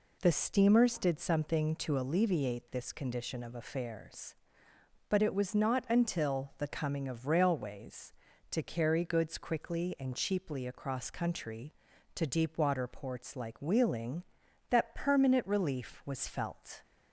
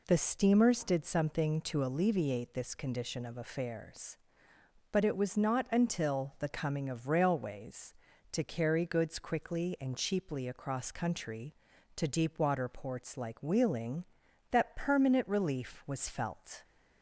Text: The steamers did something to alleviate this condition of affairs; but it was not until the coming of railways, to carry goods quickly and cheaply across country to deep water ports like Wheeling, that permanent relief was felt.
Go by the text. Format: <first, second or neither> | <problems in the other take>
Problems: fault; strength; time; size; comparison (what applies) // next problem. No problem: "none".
neither | none